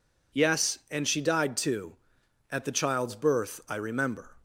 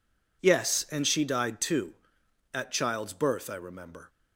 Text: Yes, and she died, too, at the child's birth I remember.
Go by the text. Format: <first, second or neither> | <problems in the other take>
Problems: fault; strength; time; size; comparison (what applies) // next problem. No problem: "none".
first | skips "the"; at 2.7 s